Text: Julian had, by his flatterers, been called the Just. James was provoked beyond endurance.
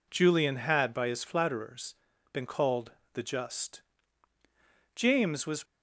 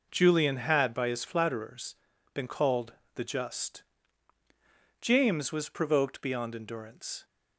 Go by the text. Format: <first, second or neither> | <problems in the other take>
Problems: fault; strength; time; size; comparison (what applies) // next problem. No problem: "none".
second | pauses between "called" and "the"; slight; at 2.9 s; 0.22 s long; slight in the second // stops before "provoked beyond endurance"; at 5.6 s